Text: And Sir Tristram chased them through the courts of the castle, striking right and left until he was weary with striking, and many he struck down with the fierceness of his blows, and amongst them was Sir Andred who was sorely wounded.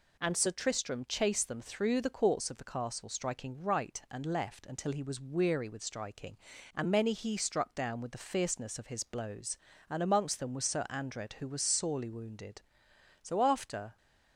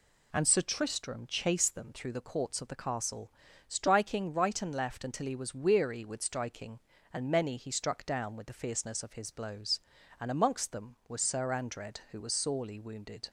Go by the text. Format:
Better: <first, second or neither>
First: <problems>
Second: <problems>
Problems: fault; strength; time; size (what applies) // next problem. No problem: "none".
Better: second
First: goes on to say "So after"; noticeable; from 13.2 s on; 0.76 s long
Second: none